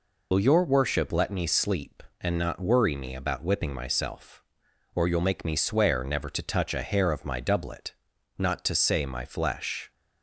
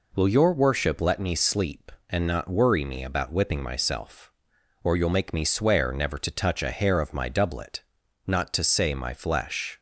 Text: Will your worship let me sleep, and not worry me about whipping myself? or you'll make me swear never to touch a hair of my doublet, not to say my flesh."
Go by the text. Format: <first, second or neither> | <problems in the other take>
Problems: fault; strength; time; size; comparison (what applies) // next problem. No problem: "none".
second | loses the start of "Will"; at 0.3 s; 65 ms